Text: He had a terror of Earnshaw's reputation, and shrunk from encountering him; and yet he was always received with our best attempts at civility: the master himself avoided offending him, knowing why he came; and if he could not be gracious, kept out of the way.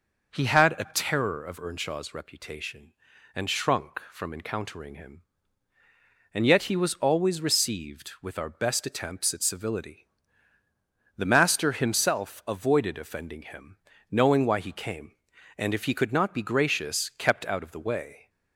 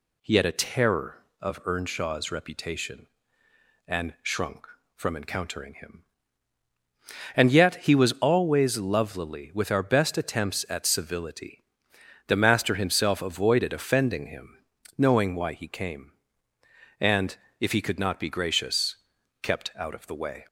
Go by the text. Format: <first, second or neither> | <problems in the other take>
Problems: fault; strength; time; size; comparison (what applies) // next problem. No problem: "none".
first | says "lovelily" for "received"; at 8.7 s // pauses between "and" and "if"; slight; at 17.3 s; 0.20 s long